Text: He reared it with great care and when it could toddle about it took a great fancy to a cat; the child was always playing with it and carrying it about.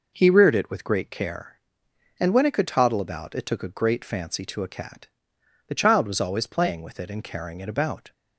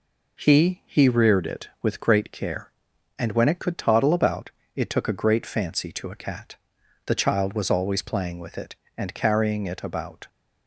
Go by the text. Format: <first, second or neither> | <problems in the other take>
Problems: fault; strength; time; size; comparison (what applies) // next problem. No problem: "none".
first | says "He" twice; at 0.8 s // pauses between "about" and "it"; slight; at 4.4 s; 0.26 s long